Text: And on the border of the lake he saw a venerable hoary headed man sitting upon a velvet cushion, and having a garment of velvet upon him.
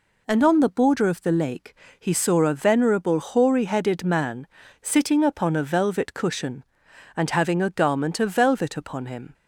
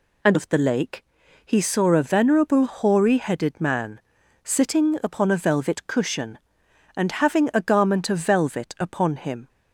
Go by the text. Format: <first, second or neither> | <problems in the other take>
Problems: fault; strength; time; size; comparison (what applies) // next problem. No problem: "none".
first | skips "on the border"; at 0.3 s // pauses between "lake" and "he"; at 1.0 s; 0.40 s long; slight in the first // pauses between "man" and "sitting"; at 4.0 s; 0.44 s long; slight in the first